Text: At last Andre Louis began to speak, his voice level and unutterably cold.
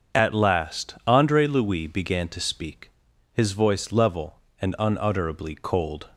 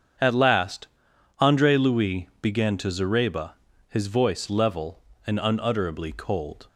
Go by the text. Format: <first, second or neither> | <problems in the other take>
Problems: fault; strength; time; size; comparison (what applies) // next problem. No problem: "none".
first | starts louder than the rest; strong; until 1.7 s; 7.5 dB; also in the first // pauses between "last" and "Andre"; noticeable; at 0.8 s; 0.50 s long // says "zareba" for "speak"; at 2.8 s